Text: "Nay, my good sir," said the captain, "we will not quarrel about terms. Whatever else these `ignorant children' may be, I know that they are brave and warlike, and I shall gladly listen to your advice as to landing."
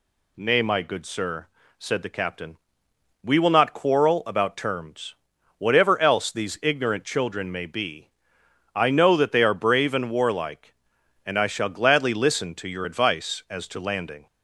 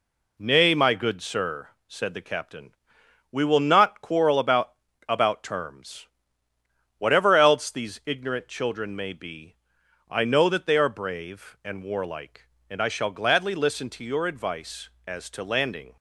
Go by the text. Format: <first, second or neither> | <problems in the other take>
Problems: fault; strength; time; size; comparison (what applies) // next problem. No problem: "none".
first | says "about" twice; at 5.0 s